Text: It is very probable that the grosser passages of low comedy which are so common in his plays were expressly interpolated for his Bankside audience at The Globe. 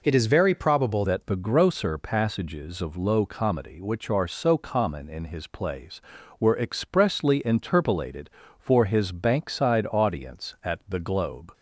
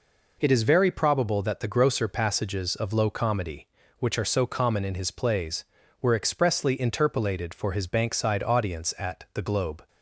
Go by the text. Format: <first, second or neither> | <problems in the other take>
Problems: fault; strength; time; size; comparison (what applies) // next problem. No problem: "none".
second | changes voice at "that"; from 1.0 s on; 10.5 s long